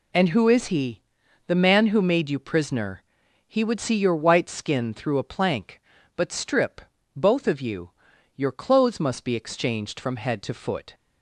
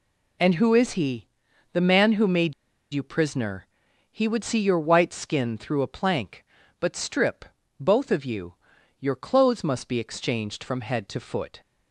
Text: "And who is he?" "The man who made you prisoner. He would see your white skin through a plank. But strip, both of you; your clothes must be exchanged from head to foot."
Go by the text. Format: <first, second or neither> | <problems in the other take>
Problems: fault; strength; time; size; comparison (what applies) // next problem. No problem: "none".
first | pauses between "made" and "you"; at 2.5 s; 0.41 s long